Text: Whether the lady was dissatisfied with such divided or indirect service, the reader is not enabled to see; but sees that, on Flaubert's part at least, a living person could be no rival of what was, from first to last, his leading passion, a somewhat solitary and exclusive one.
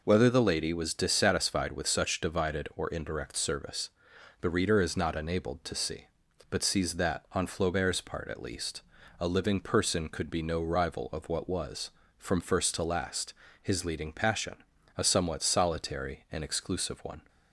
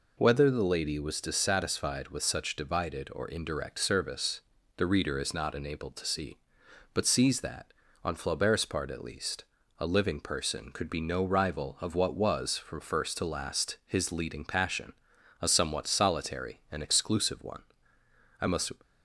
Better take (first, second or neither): first